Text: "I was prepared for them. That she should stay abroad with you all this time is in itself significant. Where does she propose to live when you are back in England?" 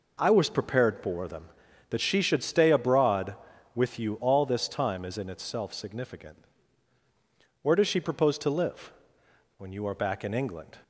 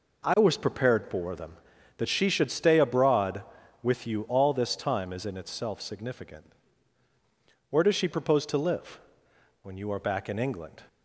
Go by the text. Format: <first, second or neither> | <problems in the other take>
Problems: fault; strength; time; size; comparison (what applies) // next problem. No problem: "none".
neither | pauses between "live" and "when"; noticeable; the same in both